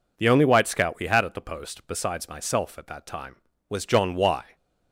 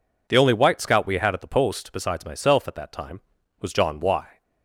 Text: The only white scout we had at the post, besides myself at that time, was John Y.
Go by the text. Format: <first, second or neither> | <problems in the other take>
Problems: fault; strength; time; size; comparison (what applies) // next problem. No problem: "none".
neither | none